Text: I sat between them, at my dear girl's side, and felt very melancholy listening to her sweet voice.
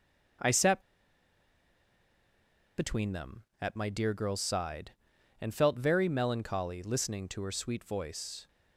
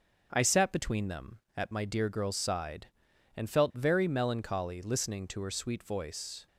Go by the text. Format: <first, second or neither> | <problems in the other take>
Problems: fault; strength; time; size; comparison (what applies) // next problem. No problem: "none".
second | starts louder than the rest; until 3.4 s; 6.5 dB; also in the second // pauses between "sat" and "between"; strong; at 0.7 s; 1.9 s long